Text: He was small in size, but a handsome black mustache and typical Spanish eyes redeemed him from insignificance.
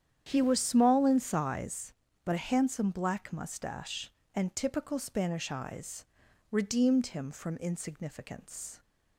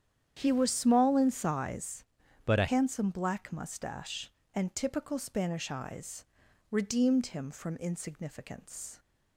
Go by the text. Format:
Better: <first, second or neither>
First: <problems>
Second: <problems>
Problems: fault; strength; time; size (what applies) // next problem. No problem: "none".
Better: first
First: starts louder than the rest; strong; until 1.3 s; 9 dB // pauses between "eyes" and "redeemed"; at 6.0 s; 0.44 s long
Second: starts louder than the rest; strong; until 1.4 s; 9.5 dB // changes voice from "but" to "a"; from 2.4 to 2.6 s; 0.2 s long // pauses between "eyes" and "redeemed"; at 6.2 s; 0.44 s long